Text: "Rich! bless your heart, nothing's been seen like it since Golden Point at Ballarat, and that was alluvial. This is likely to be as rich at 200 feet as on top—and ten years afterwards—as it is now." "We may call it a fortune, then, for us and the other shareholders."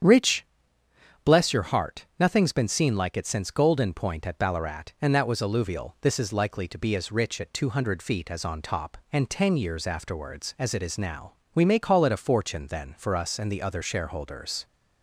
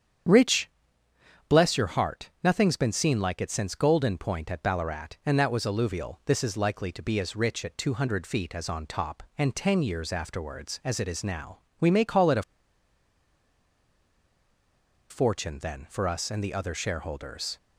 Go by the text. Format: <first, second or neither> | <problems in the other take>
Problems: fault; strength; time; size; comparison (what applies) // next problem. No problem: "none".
first | starts louder than the rest; strong; until 2.0 s; 8.5 dB; strong in the first // pauses between "a" and "fortune"; strong; at 12.4 s; 2.6 s long